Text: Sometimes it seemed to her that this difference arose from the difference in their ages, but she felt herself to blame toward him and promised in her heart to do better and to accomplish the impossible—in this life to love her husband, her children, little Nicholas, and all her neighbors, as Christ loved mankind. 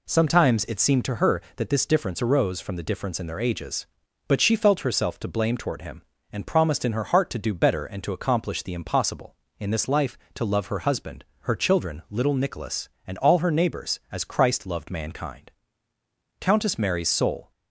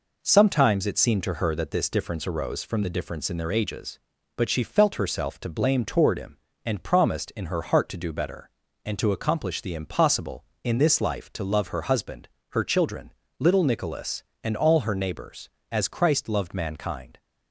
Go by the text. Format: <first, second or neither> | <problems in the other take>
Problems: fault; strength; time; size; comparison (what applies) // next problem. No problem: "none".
second | goes on to say "Countess Mary's soul"; noticeable; from 16.4 s on; 1.1 s long